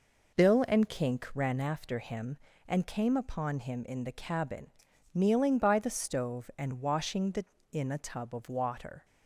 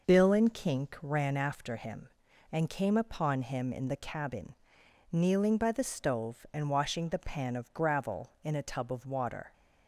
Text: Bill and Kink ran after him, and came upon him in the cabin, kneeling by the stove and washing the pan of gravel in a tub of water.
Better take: second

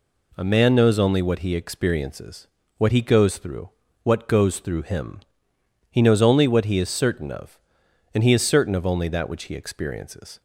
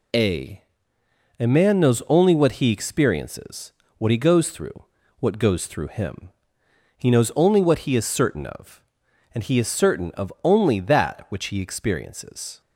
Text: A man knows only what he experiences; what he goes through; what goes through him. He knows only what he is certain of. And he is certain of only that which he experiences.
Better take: first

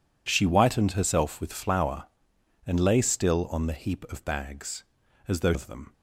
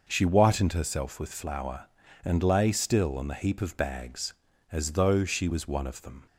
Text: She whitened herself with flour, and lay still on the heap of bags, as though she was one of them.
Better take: second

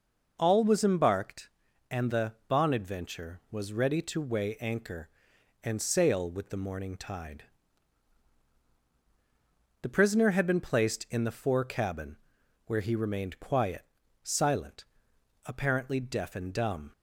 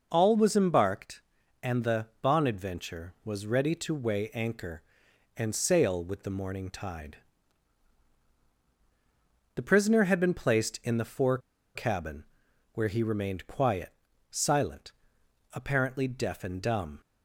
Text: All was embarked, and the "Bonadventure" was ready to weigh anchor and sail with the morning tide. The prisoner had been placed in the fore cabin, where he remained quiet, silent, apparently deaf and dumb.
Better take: first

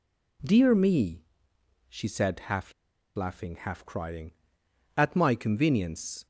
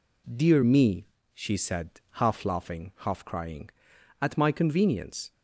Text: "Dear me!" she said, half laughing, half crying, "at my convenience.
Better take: second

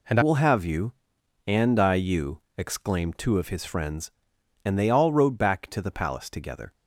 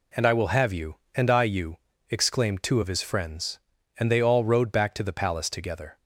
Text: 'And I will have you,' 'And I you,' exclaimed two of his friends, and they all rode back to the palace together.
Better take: second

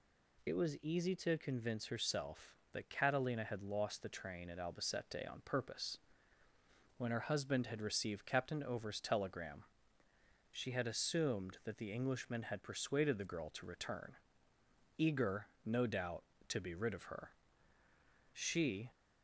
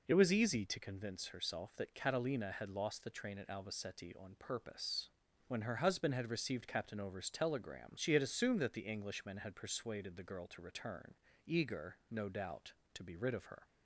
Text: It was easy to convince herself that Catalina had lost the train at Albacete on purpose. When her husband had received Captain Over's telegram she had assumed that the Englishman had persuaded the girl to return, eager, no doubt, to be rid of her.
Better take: second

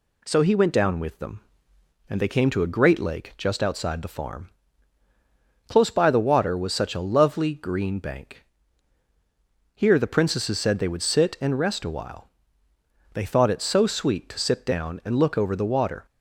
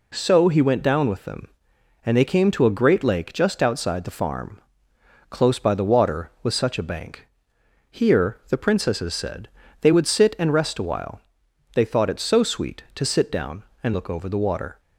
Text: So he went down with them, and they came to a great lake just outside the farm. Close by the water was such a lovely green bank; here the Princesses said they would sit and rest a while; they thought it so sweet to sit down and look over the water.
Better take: first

